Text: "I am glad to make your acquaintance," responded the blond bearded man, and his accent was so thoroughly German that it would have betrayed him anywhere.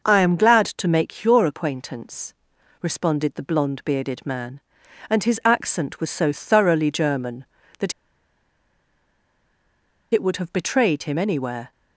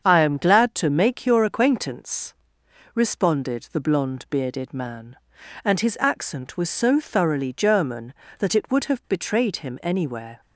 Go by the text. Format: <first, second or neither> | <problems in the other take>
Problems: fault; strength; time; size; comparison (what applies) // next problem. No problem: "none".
second | starts louder than the rest; noticeable; until 1.0 s; 6 dB; strong in the second // pauses between "that" and "it"; strong; at 7.9 s; 2.2 s long